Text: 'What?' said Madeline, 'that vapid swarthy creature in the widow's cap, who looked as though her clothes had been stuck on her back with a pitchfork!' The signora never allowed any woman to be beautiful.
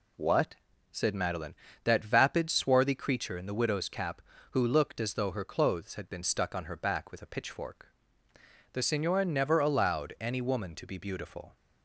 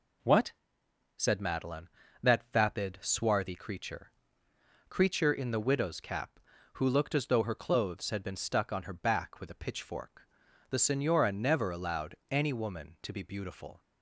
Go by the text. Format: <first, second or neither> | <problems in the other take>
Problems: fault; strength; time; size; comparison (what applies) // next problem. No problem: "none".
first | says "creature" twice; at 4.8 s